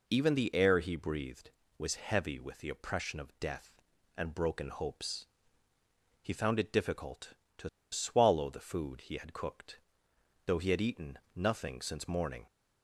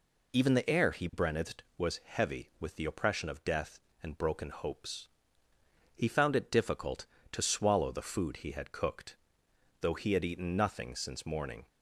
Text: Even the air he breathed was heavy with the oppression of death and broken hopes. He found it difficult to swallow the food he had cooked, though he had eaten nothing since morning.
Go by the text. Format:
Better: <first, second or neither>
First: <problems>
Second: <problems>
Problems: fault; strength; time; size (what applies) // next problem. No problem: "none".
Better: second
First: pauses between "to" and "swallow"; slight; at 7.6 s; 0.23 s long // pauses between "eaten" and "nothing"; slight; at 11.1 s; 0.18 s long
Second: none